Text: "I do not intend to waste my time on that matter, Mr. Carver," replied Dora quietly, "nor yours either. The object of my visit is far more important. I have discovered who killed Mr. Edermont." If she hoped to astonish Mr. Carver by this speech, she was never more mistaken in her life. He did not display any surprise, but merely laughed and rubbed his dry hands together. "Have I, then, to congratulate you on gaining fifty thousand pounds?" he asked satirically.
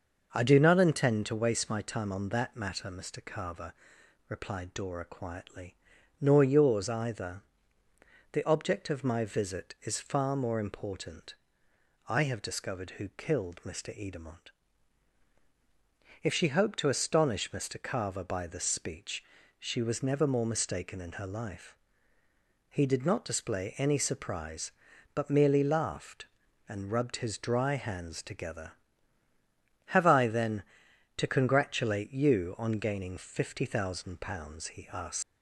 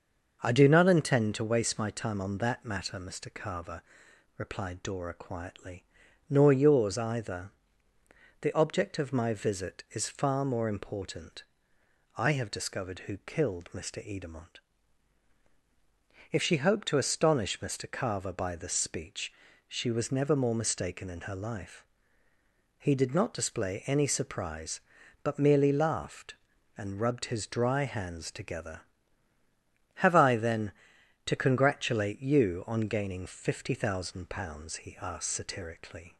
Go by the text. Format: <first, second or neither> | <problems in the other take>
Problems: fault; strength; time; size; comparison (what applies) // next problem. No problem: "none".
second | starts louder than the rest; noticeable; until 1.3 s; 6 dB; noticeable in the second // stops before "satirically"; at 35.2 s